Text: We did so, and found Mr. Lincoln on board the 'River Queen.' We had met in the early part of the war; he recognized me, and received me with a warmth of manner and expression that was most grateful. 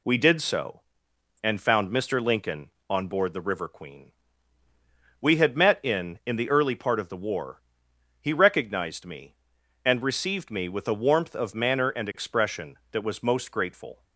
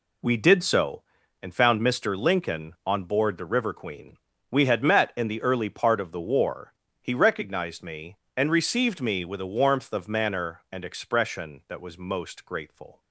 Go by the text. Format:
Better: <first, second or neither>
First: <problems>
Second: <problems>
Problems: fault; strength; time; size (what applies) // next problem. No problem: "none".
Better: second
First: says "in" twice; at 6.2 s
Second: none